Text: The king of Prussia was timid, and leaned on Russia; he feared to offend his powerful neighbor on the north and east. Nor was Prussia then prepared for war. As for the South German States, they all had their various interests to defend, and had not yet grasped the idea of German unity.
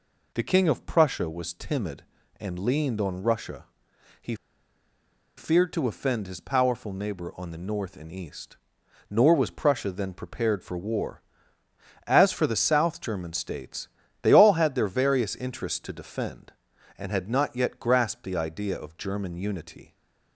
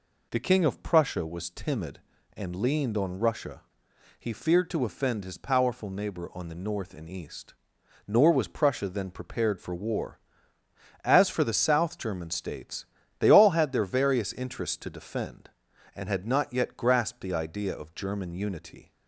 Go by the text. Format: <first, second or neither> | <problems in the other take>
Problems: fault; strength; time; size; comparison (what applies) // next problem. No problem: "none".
second | pauses between "he" and "feared"; at 4.3 s; 1.0 s long